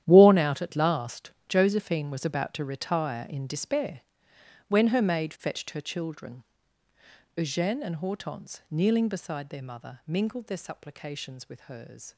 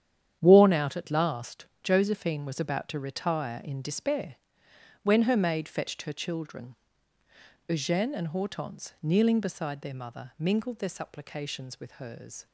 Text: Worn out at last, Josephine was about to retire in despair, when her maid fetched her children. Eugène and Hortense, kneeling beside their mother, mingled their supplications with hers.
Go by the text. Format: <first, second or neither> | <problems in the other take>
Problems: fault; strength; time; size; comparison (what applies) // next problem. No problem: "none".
second | gets quieter; strong; throughout; 14.5 dB // starts louder than the rest; strong; until 1.0 s; 11 dB; strong in the second